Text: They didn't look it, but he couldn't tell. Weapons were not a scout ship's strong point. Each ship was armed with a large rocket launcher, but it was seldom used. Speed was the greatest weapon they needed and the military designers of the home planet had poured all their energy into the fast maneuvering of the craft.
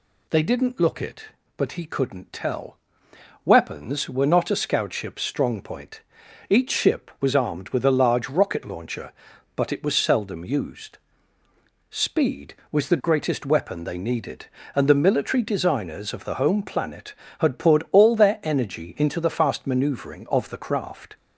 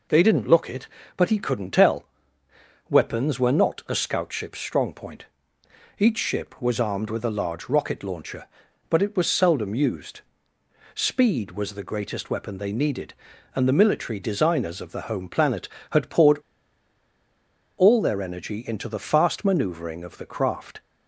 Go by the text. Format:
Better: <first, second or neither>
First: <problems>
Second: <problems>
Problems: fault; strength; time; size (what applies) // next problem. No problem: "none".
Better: first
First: none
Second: pauses between "poured" and "all"; strong; at 16.3 s; 1.4 s long